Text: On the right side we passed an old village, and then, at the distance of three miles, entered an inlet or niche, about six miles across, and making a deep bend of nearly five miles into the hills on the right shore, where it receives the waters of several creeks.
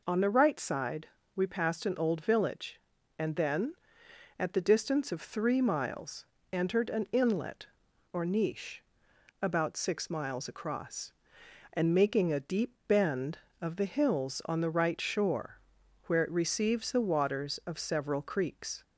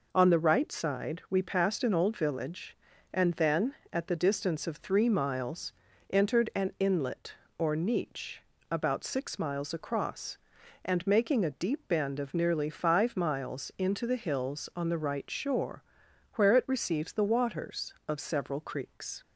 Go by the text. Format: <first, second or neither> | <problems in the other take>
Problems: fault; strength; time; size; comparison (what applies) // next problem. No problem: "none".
second | pauses between "side" and "we"; slight; at 1.0 s; 0.30 s long // skips "nearly five miles into"; at 13.7 s